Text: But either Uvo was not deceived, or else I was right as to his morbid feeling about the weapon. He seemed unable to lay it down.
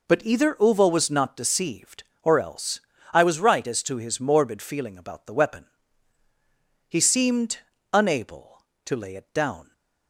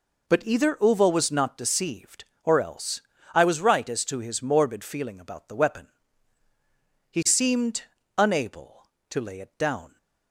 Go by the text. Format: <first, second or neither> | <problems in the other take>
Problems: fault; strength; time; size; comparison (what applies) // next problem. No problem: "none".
neither | pauses between "else" and "I"; slight; the same in both // pauses between "seemed" and "unable"; slight; the same in both